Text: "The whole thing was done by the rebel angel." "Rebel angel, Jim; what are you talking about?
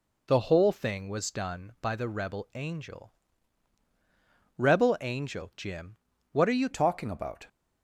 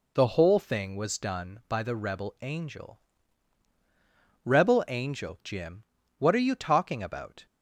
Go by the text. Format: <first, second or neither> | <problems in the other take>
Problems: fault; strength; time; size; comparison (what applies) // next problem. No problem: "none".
second | changes voice at "talking"; from 6.7 s on; 0.7 s long